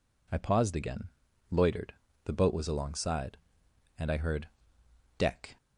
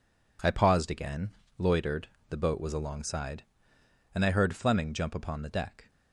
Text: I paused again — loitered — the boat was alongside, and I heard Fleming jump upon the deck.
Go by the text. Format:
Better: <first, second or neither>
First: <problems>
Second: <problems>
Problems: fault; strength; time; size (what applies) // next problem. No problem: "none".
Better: second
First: skips "Fleming jump upon the"; at 4.8 s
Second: none